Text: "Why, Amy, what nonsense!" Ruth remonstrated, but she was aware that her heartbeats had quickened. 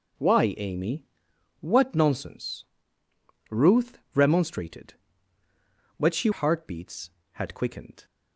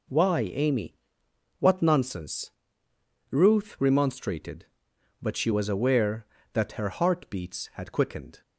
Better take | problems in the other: second | pauses between "Ruth" and "remonstrated"; slight; at 3.9 s; 0.16 s long // skips "was aware that her"; at 6.3 s

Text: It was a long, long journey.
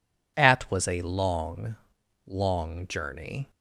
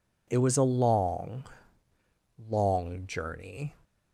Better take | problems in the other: second | says "At" for "It"; at 0.3 s

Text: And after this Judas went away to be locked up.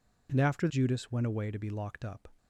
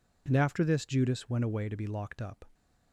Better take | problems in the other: second | skips "this"; at 0.6 s

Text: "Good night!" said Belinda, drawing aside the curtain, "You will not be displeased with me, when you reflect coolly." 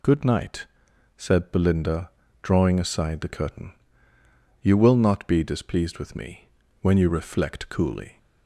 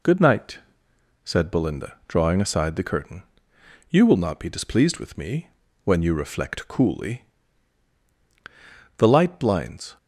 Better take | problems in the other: first | goes on to say "The light blinds"; noticeable; from 8.9 s on; 1.0 s long

